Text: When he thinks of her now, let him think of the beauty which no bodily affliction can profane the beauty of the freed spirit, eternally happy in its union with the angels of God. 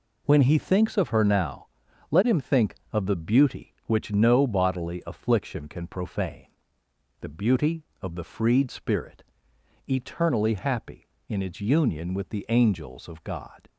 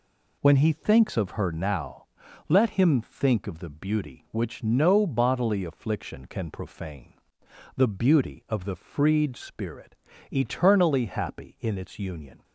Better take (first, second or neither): first